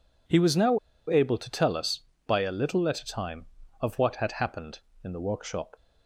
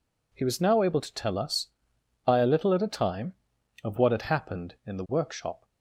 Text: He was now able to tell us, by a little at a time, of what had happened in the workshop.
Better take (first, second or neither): second